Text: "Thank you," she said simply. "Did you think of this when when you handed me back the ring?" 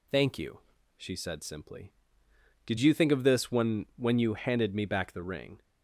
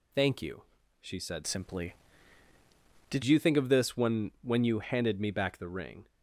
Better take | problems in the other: first | changes voice from "simply" to "Did"; from 1.4 to 3.2 s; 1.8 s long

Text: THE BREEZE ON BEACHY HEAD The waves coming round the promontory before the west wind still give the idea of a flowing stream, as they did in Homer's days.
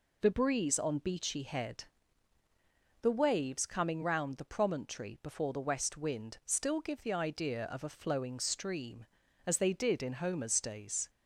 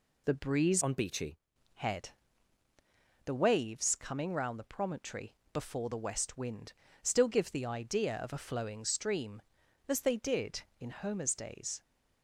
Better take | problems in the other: first | changes voice from "ON" to "BEACHY"; from 0.8 to 1.3 s; 0.5 s long // pauses between "HEAD" and "The"; at 2.0 s; 1.1 s long; also in the first // pauses between "promontory" and "before"; slight; at 5.3 s; 0.18 s long // pauses between "wind" and "still"; slight; at 6.7 s; 0.30 s long

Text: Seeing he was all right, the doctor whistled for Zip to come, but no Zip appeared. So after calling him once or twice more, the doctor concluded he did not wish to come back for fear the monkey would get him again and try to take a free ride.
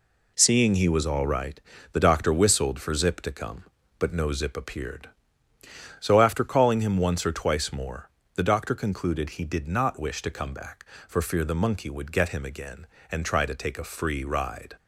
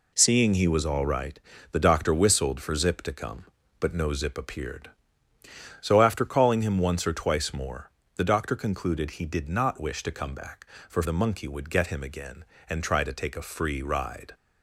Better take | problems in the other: first | skips "fear"; at 11.0 s

